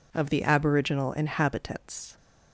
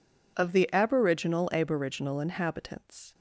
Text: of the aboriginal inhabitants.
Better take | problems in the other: first | says "aboriginal" twice; at 1.5 s

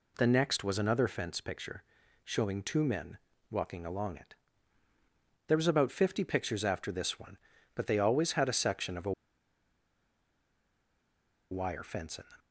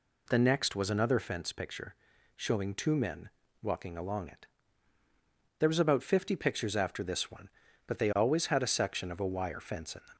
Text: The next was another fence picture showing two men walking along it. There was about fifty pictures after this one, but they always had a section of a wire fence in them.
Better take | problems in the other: second | pauses between "picture" and "showing"; at 1.8 s; 0.40 s long; also in the second // pauses between "men" and "walking"; slight; at 3.1 s; 0.34 s long; slight in the second // pauses between "a" and "wire"; strong; at 9.1 s; 2.3 s long

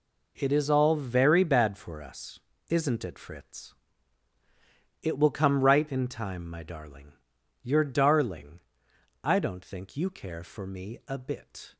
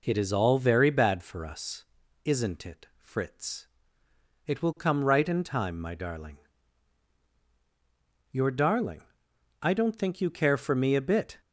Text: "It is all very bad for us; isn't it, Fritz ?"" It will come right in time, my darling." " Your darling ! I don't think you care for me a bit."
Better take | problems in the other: neither | none

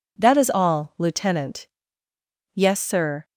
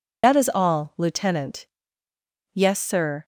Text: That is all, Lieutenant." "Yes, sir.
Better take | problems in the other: first | loses the start of "That"; at 0.2 s; 65 ms

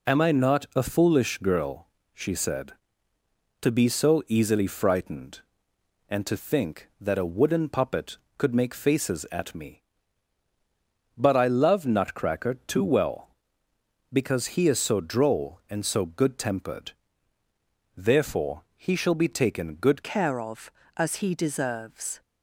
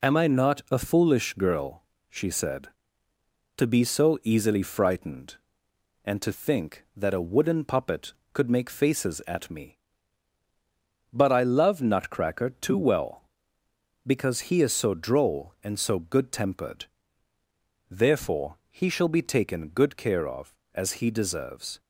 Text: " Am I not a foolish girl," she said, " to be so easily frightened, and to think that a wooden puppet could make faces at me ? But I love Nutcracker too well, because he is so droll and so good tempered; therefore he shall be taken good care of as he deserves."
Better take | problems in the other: second | changes voice at "care"; from 20.0 s on; 2.2 s long

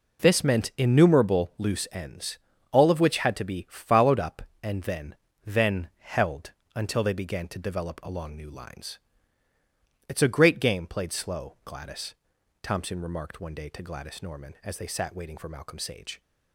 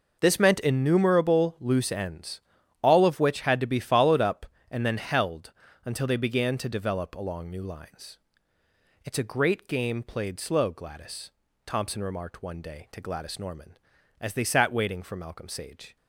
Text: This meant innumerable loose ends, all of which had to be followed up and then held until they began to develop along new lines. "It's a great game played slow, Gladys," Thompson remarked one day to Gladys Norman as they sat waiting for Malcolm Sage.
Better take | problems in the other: second | says "then" twice; at 5.4 s // pauses between "held" and "until"; slight; at 6.5 s; 0.24 s long; slight in the second

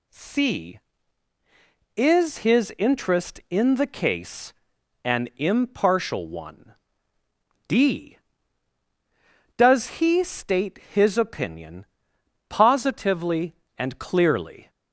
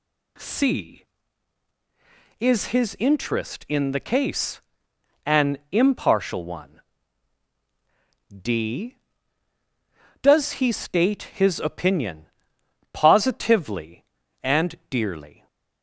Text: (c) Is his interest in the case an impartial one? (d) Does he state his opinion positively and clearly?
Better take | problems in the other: first | pauses between "case" and "an"; noticeable; at 4.6 s; 0.64 s long; noticeable in the first // pauses between "opinion" and "positively"; noticeable; at 12.2 s; 0.66 s long; noticeable in the first // says "dearly" for "clearly"; at 14.8 s

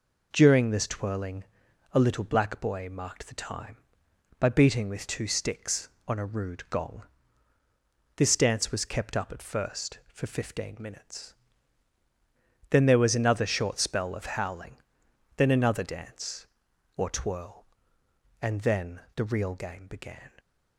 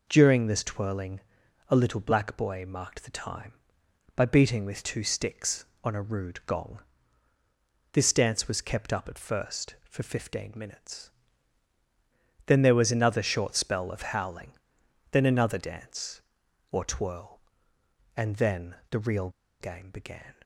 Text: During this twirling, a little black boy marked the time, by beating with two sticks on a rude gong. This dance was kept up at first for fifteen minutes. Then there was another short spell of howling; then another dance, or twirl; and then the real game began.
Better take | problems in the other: first | pauses between "then" and "the"; slight; at 18.7 s; 0.16 s long; slight in the first // pauses between "real" and "game"; slight; at 19.2 s; 0.31 s long

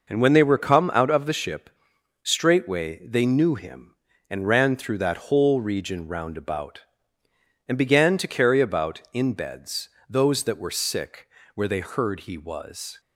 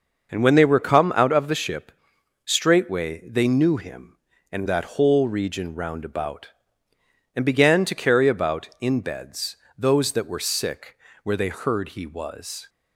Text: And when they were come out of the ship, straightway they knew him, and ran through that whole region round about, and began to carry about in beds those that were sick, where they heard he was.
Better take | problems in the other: first | starts louder than the rest; until 1.3 s; 6 dB // skips "ran through"; at 4.6 s // pauses between "beds" and "those"; slight; at 9.5 s; 0.20 s long; slight in the first

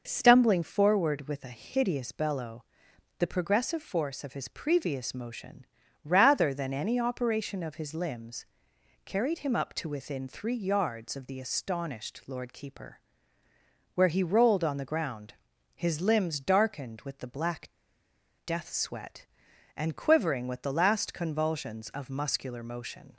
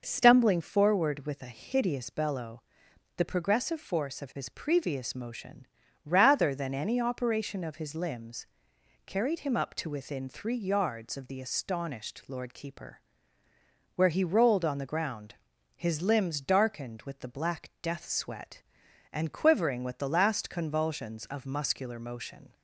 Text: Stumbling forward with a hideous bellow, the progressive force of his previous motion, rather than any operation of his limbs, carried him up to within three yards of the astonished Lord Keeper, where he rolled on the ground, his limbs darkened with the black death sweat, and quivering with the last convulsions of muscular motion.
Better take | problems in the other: second | pauses between "black" and "death"; noticeable; at 17.6 s; 0.76 s long

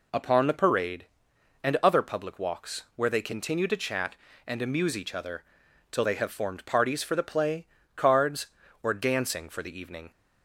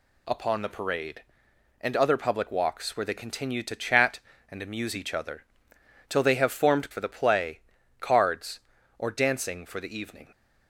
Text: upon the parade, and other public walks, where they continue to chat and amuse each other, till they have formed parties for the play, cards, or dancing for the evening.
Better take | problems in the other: first | skips "parties"; at 6.9 s

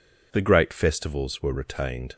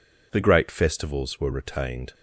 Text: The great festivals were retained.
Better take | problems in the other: neither | none

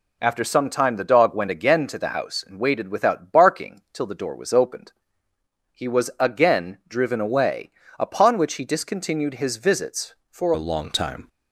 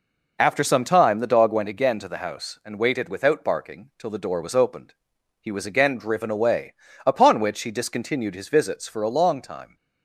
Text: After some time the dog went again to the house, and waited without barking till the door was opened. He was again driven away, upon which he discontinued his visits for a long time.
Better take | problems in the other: second | changes voice at "a"; from 10.5 s on; 0.7 s long

